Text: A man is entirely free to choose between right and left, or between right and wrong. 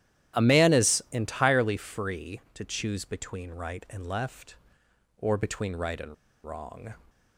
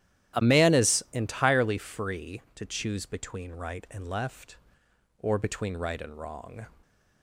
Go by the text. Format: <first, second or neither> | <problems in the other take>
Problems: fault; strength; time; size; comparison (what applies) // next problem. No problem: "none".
second | starts louder than the rest; strong; until 1.4 s; 12 dB; strong in the second // pauses between "and" and "wrong"; slight; at 6.1 s; 0.30 s long